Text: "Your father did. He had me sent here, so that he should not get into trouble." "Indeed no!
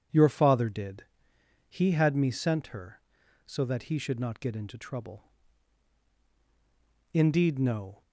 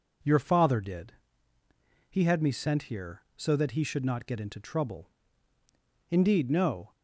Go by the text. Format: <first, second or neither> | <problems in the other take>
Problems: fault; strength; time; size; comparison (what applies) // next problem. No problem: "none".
second | says "her" for "here"; at 2.6 s